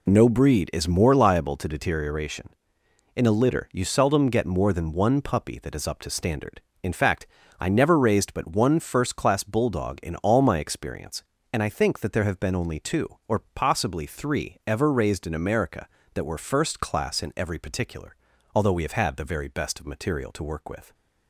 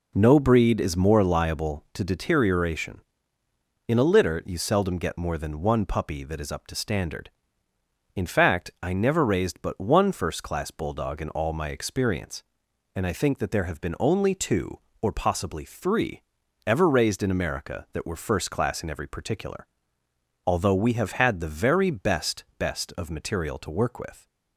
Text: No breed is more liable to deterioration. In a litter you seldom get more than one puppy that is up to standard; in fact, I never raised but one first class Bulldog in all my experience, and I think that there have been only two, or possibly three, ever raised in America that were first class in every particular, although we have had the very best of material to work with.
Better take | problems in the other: first | says "best" twice; at 22.5 s

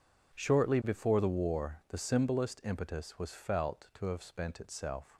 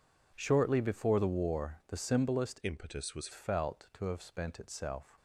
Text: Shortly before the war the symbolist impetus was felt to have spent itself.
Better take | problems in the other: first | changes voice from "impetus" to "was"; from 2.6 to 3.2 s; 0.6 s long

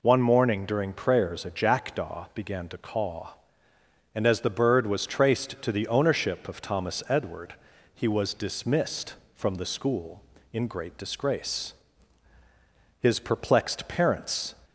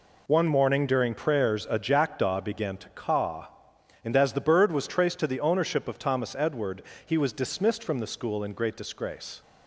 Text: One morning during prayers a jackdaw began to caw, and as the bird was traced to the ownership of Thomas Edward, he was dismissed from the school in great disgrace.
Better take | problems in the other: second | goes on to say "His perplexed parents"; from 13.0 s on; 1.5 s long

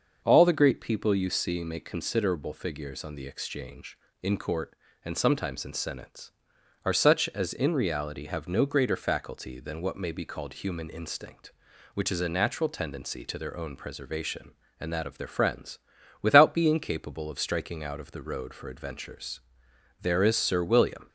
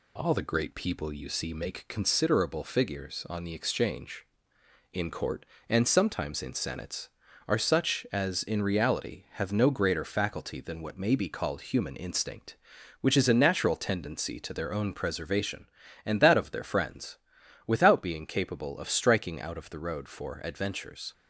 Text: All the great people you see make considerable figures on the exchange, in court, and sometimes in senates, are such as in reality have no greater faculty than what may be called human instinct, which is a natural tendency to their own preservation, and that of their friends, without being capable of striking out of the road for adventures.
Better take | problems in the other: second | starts louder than the rest; until 1.2 s; 6 dB // goes on to say "There is Sir William"; noticeable; from 20.0 s on; 1.0 s long

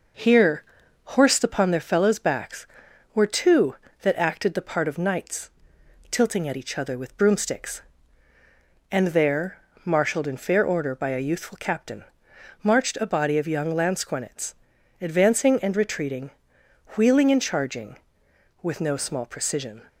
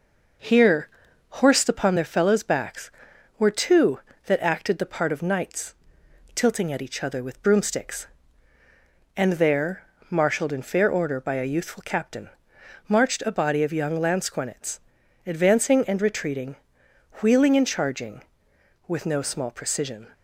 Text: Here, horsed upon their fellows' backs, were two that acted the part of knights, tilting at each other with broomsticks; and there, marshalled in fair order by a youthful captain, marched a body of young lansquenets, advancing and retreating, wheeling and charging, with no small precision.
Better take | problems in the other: neither | none

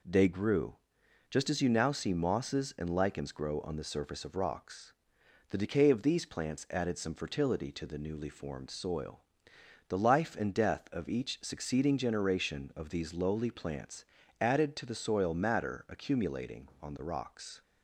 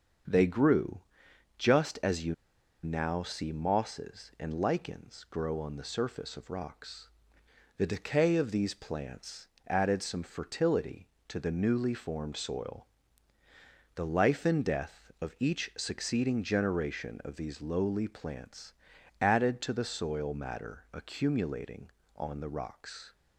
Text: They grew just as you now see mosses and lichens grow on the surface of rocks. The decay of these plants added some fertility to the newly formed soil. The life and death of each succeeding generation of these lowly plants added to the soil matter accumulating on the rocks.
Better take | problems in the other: first | starts louder than the rest; until 1.8 s; 7 dB // pauses between "grew" and "just"; noticeable; at 1.0 s; 0.56 s long; noticeable in the first // pauses between "you" and "now"; noticeable; at 2.3 s; 0.50 s long // pauses between "plants" and "added"; slight; at 9.4 s; 0.20 s long // pauses between "plants" and "added"; noticeable; at 18.7 s; 0.48 s long; slight in the first

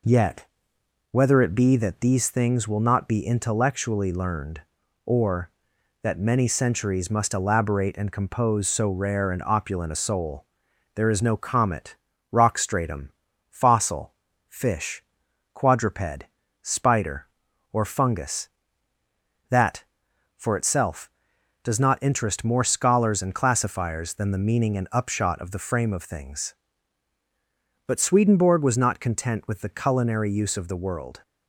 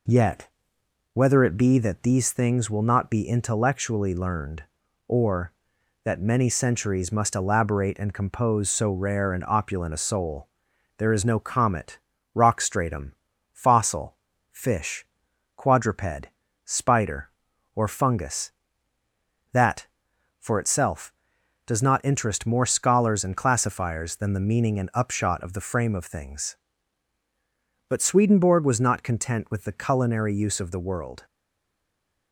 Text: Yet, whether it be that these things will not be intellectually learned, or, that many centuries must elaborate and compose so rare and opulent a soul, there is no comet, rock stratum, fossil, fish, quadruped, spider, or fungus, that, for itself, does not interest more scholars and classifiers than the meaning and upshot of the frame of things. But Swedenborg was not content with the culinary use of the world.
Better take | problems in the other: first | stays silent after the last word; from 31.2 s on; 1.1 s long

